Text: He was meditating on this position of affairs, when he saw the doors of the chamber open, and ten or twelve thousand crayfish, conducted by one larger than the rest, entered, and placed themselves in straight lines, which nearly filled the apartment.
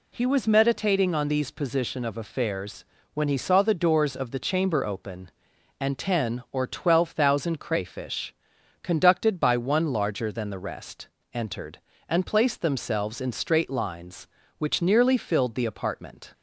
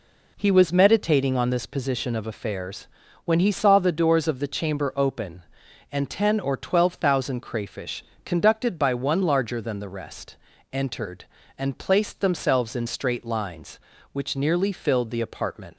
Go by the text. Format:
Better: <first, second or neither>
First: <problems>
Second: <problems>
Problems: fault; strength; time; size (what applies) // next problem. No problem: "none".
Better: second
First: says "these" for "this"; at 1.2 s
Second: none